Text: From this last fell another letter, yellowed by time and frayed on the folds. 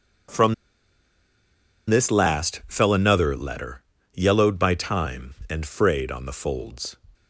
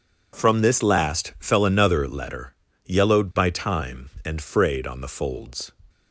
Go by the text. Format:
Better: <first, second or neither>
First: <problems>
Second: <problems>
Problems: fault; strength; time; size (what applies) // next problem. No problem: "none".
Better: second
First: pauses between "From" and "this"; strong; at 0.5 s; 1.3 s long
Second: none